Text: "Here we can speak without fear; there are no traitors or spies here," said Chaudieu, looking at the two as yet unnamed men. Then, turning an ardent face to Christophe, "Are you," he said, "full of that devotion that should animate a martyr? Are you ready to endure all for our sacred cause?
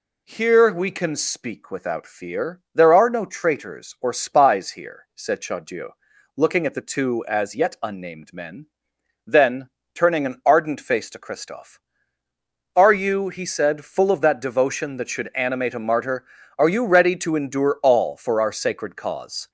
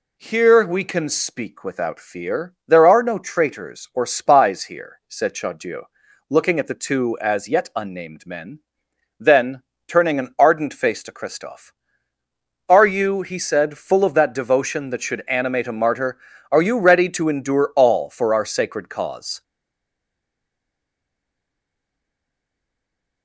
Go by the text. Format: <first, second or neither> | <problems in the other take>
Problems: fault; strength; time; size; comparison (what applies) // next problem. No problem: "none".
first | stays silent after the last word; strong; from 19.4 s on; 3.8 s long